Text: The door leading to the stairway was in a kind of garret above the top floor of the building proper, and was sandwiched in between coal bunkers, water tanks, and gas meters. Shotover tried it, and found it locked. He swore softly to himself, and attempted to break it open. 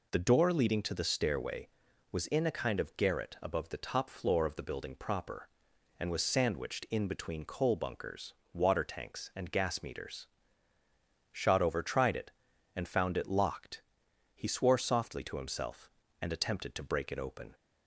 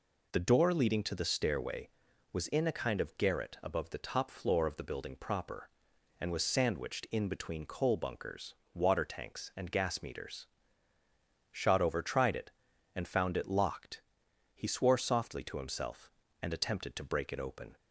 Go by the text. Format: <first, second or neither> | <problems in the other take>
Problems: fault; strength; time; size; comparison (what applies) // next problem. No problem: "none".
neither | none